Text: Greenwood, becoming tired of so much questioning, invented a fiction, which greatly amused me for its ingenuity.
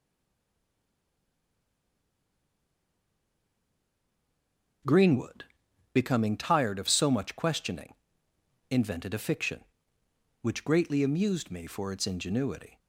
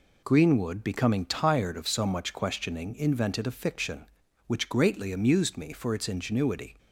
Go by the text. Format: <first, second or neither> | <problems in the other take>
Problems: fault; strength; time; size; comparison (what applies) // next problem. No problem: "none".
second | stays silent before the first word; strong; until 4.8 s; 4.8 s long